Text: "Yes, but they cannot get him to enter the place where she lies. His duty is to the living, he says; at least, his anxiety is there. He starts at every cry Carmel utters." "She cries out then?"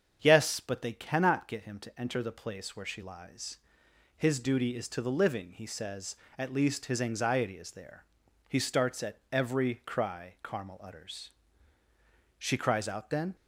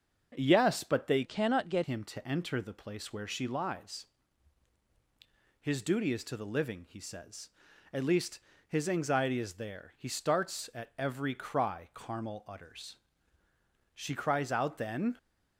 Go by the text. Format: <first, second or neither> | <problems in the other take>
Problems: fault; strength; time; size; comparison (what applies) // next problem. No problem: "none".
first | starts louder than the rest; until 1.3 s; 6.5 dB; strong in the first // changes voice from "cannot" to "get"; from 1.2 to 1.8 s; 0.6 s long